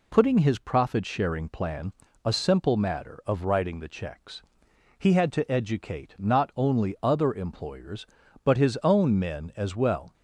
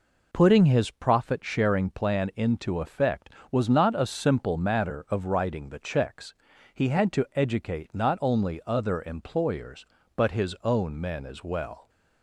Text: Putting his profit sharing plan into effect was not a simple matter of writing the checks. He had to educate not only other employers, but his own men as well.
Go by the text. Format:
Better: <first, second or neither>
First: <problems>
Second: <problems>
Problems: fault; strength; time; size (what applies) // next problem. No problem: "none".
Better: second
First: skips "into effect was not"; at 2.0 s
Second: none